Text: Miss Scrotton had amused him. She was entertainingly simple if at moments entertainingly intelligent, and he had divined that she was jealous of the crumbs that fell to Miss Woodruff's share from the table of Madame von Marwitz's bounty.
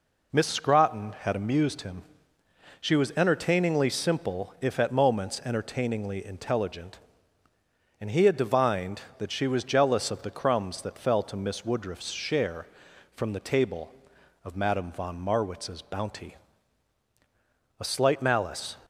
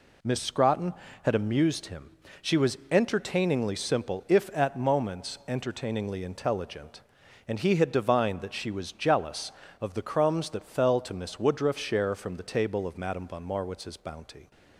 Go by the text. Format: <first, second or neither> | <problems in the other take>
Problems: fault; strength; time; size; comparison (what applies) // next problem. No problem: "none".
second | goes on to say "A slight malice"; noticeable; from 17.7 s on; 0.96 s long